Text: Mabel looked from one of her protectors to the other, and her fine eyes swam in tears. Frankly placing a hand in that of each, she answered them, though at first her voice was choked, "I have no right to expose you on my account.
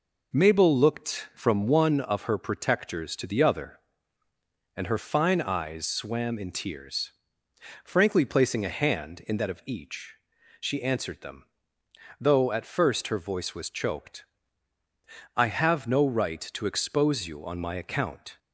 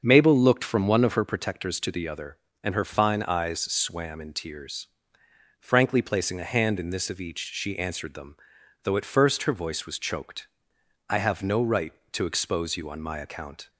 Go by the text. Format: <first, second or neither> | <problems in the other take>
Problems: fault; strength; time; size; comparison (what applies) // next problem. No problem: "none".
first | starts louder than the rest; until 1.0 s; 6.5 dB // says "this" for "that"; at 6.8 s